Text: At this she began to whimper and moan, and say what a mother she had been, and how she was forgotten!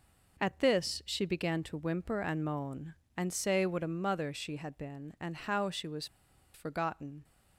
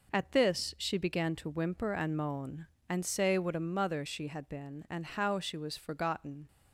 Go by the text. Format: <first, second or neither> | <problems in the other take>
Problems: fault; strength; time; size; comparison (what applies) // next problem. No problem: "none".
second | pauses between "was" and "forgotten"; noticeable; at 6.0 s; 0.48 s long